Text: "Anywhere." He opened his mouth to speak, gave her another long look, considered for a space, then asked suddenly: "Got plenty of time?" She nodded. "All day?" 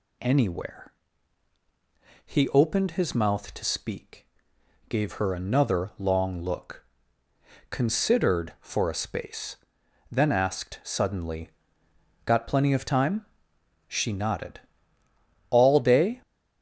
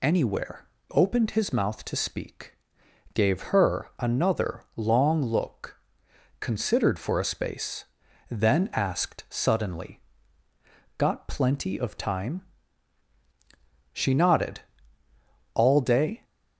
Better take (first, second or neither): first